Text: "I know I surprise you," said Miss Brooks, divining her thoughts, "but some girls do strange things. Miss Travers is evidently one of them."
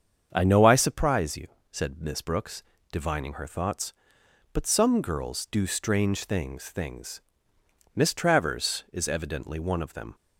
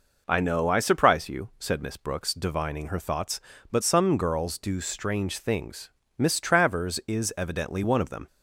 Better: second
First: starts louder than the rest; strong; until 1.3 s; 7.5 dB // says "things" twice; at 6.6 s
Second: none

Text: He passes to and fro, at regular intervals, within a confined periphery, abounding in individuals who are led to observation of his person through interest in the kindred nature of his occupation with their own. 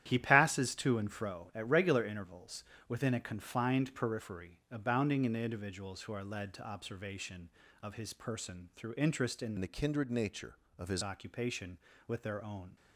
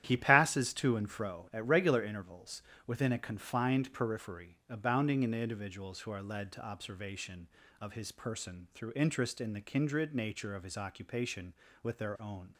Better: second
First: starts louder than the rest; strong; until 1.0 s; 11.5 dB // changes voice from "the" to "his"; from 9.5 to 11.0 s; 1.5 s long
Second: starts louder than the rest; strong; until 1.0 s; 11.5 dB

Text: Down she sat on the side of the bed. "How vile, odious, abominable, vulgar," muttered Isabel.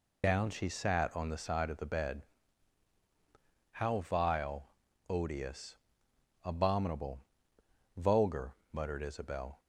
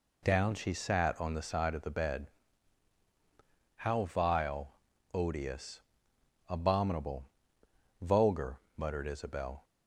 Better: second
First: loses the start of "Down"; at 0.2 s; 55 ms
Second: none

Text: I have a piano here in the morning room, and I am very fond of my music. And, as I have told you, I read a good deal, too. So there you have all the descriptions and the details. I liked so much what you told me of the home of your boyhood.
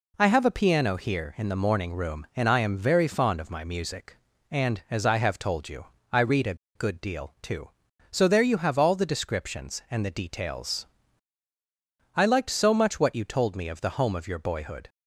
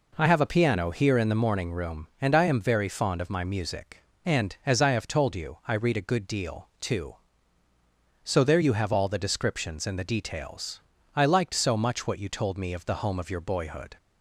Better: second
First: pauses between "a" and "good"; slight; at 6.5 s; 0.20 s long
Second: none

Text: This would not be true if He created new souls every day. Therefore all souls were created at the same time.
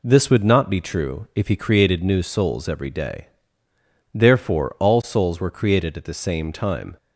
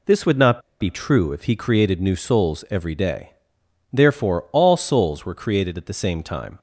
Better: first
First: none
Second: pauses between "not" and "be"; slight; at 0.5 s; 0.21 s long

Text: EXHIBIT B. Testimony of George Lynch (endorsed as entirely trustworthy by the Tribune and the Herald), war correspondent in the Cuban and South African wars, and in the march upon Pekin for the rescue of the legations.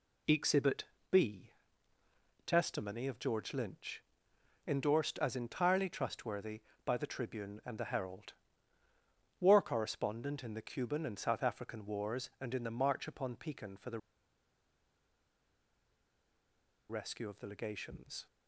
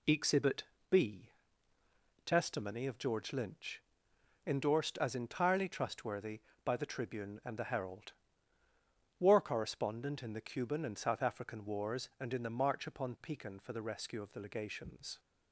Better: second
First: pauses between "EXHIBIT" and "B"; slight; at 0.8 s; 0.26 s long // pauses between "the" and "rescue"; strong; at 13.9 s; 2.9 s long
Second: pauses between "EXHIBIT" and "B"; slight; at 0.6 s; 0.26 s long

